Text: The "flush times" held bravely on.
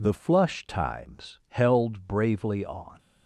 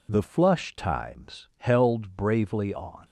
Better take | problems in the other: neither | none

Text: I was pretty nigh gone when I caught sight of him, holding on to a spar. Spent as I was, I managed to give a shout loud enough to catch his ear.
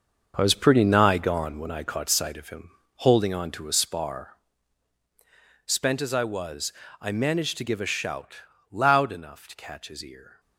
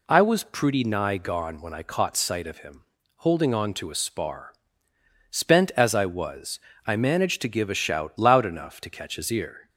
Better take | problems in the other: second | gets quieter; strong; throughout; 10 dB // pauses between "shout" and "loud"; slight; at 8.3 s; 0.34 s long

